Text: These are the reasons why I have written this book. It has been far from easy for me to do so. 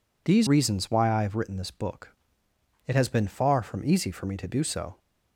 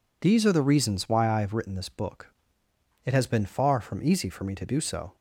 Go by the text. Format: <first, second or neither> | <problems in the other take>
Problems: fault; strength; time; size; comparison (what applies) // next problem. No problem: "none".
second | skips "are the"; at 0.4 s